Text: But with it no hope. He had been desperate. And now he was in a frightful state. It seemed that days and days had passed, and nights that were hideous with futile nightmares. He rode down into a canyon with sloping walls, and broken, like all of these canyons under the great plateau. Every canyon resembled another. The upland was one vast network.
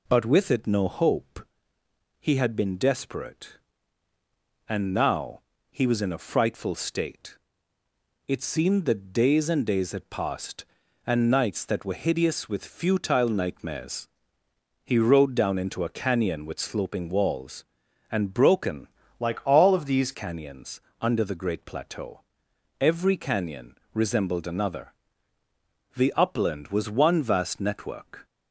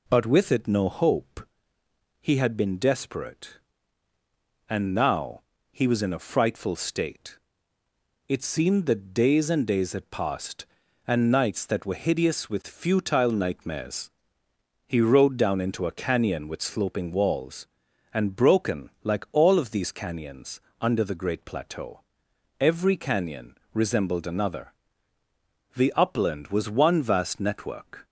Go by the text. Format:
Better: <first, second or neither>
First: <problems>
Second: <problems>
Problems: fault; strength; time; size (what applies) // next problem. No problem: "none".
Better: second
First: pauses between "now" and "he"; slight; at 5.4 s; 0.30 s long // changes voice from "like" to "these"; from 19.2 to 20.1 s; 0.9 s long // pauses between "canyons" and "under"; slight; at 20.7 s; 0.22 s long // pauses between "canyon" and "resembled"; slight; at 23.7 s; 0.18 s long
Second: pauses between "now" and "he"; slight; at 5.4 s; 0.30 s long // pauses between "canyons" and "under"; slight; at 20.5 s; 0.22 s long // pauses between "canyon" and "resembled"; slight; at 23.5 s; 0.18 s long